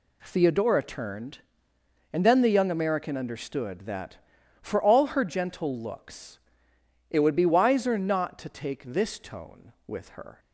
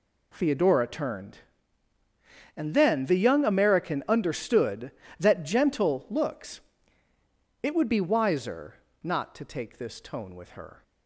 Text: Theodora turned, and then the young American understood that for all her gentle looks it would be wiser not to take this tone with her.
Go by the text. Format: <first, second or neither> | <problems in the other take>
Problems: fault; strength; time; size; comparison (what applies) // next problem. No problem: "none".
first | skips "for all her"; at 5.4 s // pauses between "looks" and "it"; at 6.6 s; 1.0 s long; noticeable in the first // pauses between "wiser" and "not"; slight; at 8.7 s; 0.30 s long